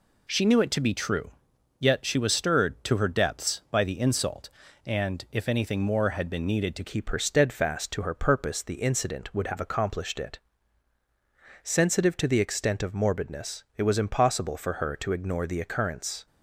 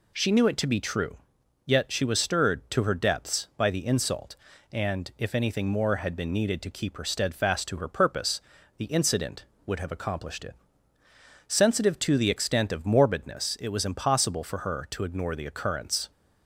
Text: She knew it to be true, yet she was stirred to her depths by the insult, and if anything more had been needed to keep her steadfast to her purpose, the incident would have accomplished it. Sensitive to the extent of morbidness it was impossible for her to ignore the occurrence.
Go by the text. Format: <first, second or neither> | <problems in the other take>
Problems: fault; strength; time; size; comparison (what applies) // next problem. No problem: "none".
second | changes voice at "keep"; from 6.8 s on; 9.4 s long